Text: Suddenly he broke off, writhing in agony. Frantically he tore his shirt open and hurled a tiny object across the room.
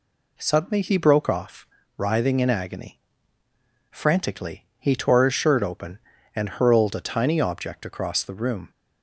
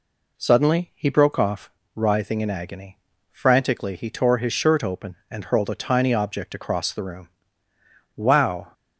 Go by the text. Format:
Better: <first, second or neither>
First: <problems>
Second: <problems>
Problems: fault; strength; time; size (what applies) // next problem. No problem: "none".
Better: first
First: none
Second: goes on to say "Wow"; from 8.1 s on; 0.56 s long